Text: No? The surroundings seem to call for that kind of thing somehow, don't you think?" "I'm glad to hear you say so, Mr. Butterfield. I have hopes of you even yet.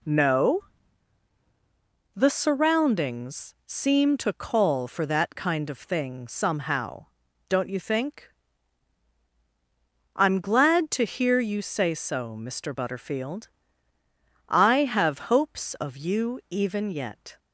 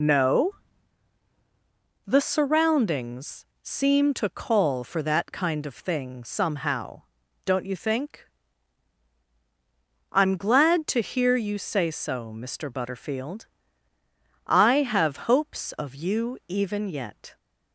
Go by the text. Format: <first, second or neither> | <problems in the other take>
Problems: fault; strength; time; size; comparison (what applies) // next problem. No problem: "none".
first | loses the start of "No"; at 0.0 s; 55 ms // pauses between "surroundings" and "seem"; slight; at 3.4 s; 0.17 s long